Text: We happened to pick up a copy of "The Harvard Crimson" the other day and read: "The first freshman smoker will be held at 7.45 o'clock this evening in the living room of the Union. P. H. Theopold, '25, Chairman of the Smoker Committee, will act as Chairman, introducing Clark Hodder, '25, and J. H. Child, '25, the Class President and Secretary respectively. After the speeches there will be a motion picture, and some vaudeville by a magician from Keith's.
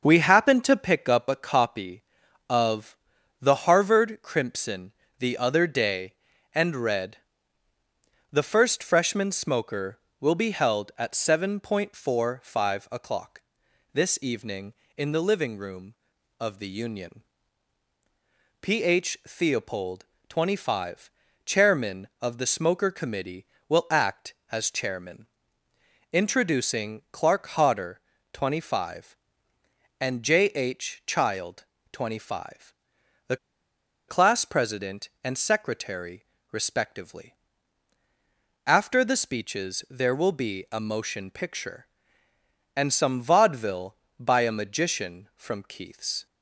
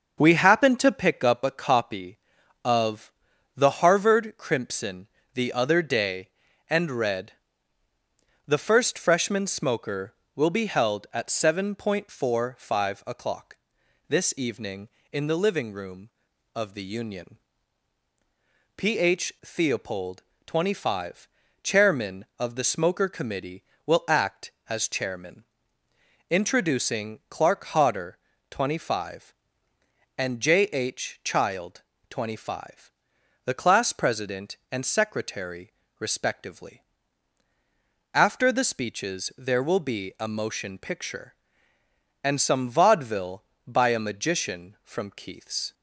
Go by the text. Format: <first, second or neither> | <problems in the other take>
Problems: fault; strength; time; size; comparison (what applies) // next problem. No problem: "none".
second | starts louder than the rest; until 1.0 s; 6.5 dB; also in the second // pauses between "of" and "The"; at 2.9 s; 0.42 s long; also in the second // pauses between "Crimson" and "the"; slight; at 4.9 s; 0.26 s long; slight in the second // pauses between "o'clock" and "this"; noticeable; at 13.3 s; 0.54 s long; noticeable in the second // pauses between "the" and "Class"; noticeable; at 33.3 s; 0.70 s long // pauses between "Secretary" and "respectively"; slight; at 36.2 s; 0.28 s long; slight in the second